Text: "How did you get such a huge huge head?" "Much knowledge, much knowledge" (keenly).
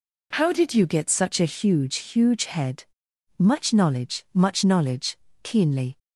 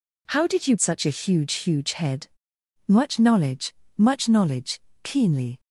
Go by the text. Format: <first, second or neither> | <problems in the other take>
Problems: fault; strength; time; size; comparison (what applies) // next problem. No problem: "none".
first | skips "get"; at 0.7 s